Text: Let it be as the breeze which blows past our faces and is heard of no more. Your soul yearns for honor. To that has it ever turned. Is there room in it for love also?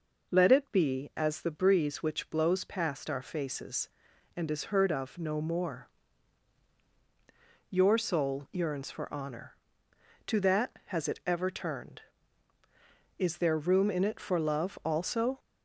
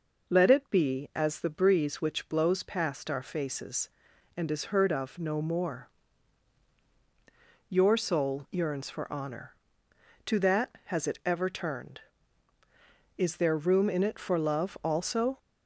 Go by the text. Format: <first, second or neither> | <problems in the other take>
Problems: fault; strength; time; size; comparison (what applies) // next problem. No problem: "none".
neither | none